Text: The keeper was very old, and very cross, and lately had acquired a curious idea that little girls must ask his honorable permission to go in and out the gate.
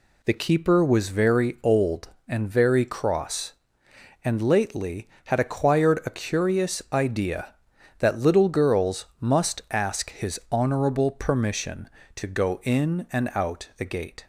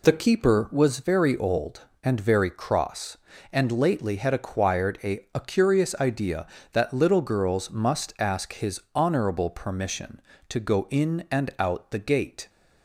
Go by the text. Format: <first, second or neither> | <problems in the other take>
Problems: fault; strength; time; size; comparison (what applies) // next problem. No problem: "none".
first | says "a" twice; at 5.3 s // pauses between "his" and "honorable"; slight; at 8.7 s; 0.16 s long